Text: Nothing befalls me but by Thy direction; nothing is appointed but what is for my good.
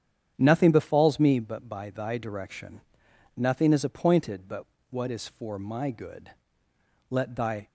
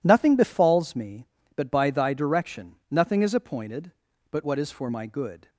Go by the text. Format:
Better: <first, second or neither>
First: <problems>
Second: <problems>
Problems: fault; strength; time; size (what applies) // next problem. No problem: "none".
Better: second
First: starts louder than the rest; strong; until 1.3 s; 8.5 dB // pauses between "but" and "what"; slight; at 4.6 s; 0.26 s long // goes on to say "Let Thy"; from 7.1 s on; 0.56 s long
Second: none